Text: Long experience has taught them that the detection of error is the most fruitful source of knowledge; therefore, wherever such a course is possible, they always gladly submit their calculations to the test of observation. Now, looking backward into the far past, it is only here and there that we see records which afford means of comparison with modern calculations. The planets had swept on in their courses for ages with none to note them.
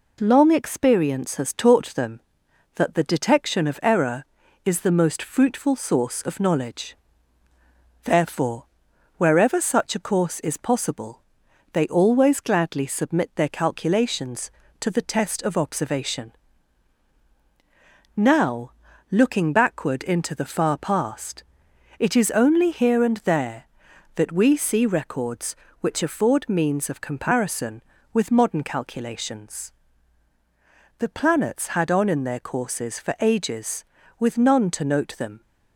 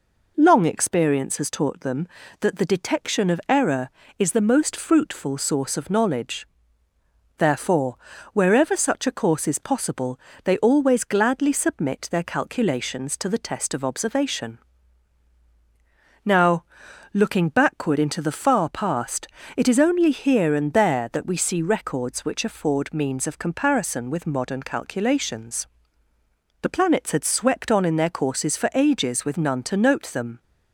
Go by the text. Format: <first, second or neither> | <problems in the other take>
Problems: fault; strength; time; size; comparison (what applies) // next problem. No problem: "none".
second | skips "swept"; at 31.9 s